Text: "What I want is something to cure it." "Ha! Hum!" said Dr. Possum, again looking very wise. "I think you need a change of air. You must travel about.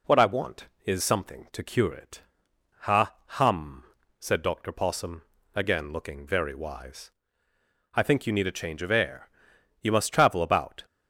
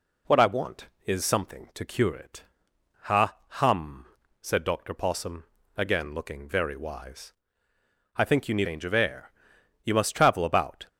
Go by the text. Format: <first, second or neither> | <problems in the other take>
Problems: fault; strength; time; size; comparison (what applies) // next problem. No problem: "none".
first | skips "a"; at 8.6 s